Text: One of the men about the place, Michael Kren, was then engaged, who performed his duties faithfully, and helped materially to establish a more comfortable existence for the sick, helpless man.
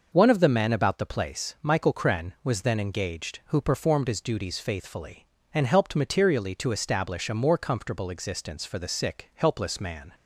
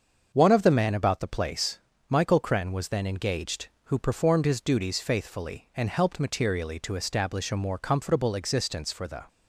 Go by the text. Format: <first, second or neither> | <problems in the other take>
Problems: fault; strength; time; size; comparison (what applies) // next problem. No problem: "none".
first | starts louder than the rest; until 1.3 s; 6.5 dB // stops before "sick helpless man"; at 9.2 s